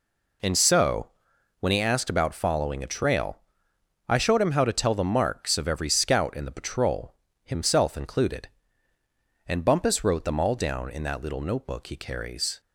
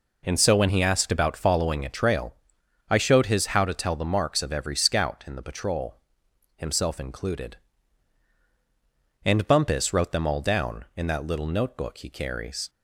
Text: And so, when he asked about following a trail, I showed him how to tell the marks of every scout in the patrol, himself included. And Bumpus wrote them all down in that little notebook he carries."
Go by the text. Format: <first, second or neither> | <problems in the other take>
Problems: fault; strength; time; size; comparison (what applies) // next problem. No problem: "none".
first | says "his" for "him"; at 3.2 s